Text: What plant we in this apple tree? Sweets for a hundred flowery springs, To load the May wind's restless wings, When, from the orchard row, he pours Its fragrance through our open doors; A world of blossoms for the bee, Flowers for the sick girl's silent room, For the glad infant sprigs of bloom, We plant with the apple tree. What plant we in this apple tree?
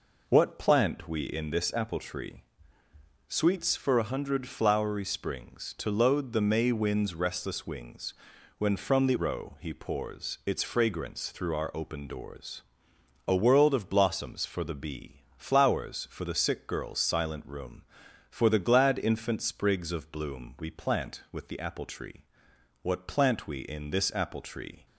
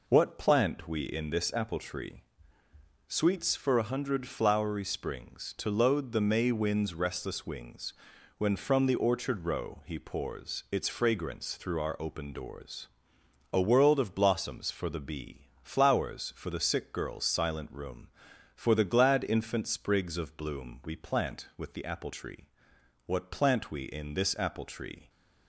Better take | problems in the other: second | skips "orchard"; at 9.1 s

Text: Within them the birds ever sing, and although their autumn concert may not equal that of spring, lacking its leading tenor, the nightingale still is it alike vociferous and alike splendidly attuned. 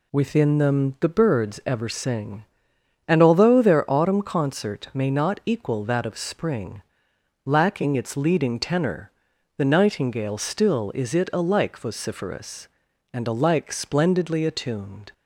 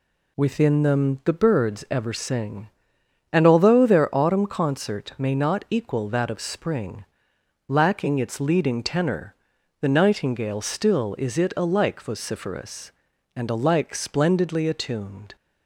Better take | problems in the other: neither | none

